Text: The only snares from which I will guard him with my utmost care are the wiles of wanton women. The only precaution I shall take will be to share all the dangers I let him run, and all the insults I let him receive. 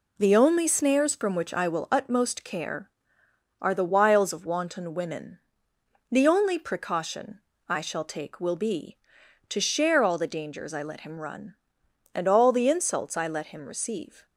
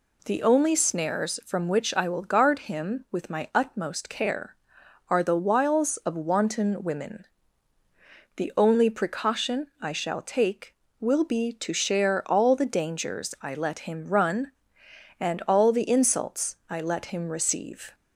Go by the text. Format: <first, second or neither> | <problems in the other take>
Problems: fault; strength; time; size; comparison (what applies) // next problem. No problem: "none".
second | skips "guard him with my"; at 1.9 s // pauses between "precaution" and "I"; slight; at 7.4 s; 0.28 s long